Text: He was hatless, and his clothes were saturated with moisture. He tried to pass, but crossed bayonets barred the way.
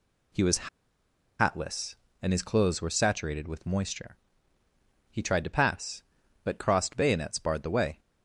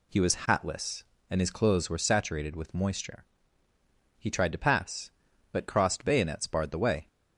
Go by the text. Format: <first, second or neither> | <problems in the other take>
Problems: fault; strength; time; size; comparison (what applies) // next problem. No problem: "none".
second | pauses between "was" and "hatless"; noticeable; at 0.6 s; 0.70 s long